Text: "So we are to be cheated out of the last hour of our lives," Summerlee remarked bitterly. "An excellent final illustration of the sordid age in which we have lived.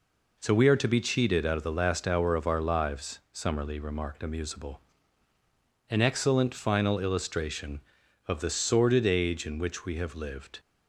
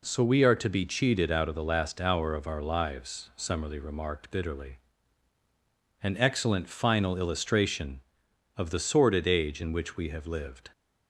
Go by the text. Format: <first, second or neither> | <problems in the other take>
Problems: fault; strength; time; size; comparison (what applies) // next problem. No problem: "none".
second | says "amusable" for "bitterly"; at 4.2 s